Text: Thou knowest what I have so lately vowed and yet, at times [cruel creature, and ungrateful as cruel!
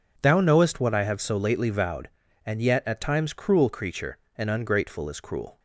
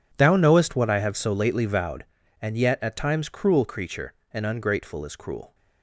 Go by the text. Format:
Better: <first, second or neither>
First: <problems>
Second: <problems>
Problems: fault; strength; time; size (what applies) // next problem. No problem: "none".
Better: first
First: none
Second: gets quieter; strong; throughout; 16.5 dB